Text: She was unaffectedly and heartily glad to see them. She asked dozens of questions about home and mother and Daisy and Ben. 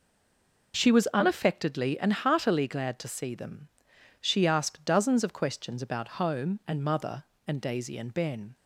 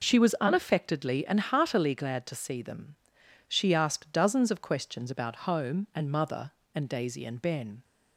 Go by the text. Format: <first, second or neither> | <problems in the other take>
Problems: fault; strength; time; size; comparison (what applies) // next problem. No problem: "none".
second | stays silent before the first word; slight; until 0.7 s; 0.7 s long